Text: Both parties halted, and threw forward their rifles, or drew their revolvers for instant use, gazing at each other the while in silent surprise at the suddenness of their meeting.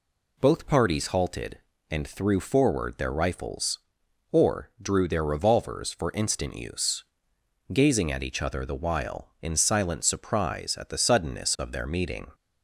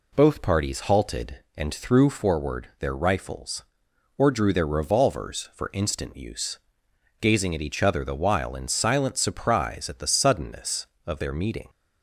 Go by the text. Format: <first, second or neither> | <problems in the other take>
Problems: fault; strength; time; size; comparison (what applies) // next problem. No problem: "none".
neither | none